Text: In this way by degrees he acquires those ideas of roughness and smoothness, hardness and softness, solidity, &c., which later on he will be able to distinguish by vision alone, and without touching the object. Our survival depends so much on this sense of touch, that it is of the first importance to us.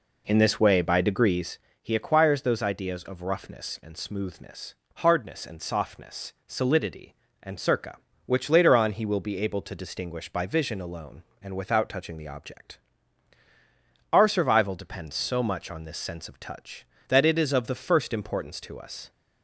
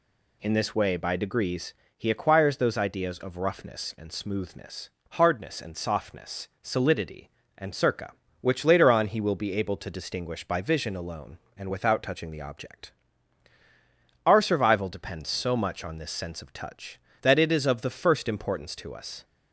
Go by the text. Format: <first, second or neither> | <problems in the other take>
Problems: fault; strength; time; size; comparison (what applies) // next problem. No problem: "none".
second | starts louder than the rest; until 1.6 s; 3.5 dB // pauses between "degrees" and "he"; slight; at 1.5 s; 0.22 s long; slight in the second